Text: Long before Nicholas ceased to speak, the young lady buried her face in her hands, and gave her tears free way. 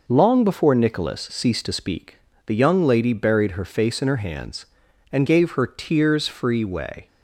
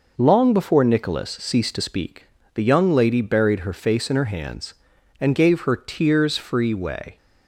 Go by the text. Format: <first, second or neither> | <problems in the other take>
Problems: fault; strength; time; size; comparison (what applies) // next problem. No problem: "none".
neither | none